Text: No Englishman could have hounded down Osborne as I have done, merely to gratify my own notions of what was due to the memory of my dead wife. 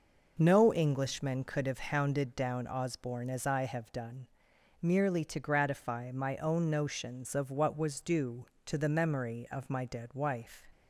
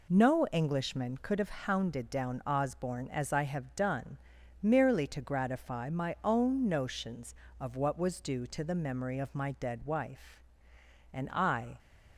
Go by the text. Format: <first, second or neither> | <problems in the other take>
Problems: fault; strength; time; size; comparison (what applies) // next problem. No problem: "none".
first | goes on to say "And I"; noticeable; from 11.1 s on; 0.68 s long